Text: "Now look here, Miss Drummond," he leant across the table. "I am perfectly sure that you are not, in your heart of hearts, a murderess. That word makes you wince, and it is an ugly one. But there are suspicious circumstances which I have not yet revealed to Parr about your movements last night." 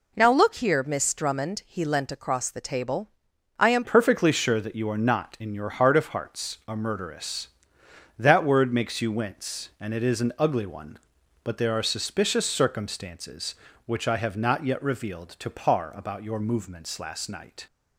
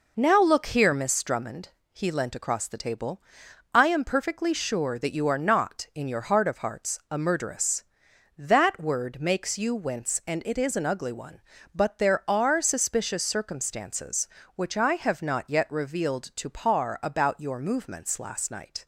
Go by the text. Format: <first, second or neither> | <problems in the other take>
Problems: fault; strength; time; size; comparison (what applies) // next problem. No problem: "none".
second | changes voice at "perfectly"; from 3.8 s on; 13.8 s long